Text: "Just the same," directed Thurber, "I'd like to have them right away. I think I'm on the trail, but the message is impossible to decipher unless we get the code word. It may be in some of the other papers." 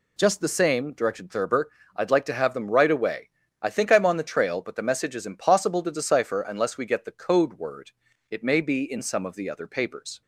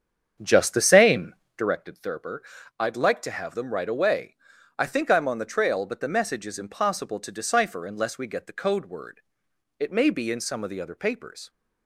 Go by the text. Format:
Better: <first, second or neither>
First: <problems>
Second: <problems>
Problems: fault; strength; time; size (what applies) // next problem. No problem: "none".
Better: first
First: none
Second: starts louder than the rest; strong; until 1.8 s; 7.5 dB